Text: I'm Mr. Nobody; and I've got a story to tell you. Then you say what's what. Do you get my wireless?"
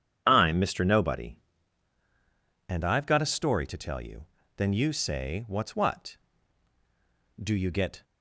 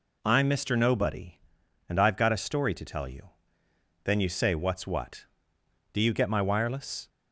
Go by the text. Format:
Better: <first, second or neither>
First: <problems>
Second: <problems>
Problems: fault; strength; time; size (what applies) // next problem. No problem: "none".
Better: second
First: stops before "my wireless"; at 8.0 s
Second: none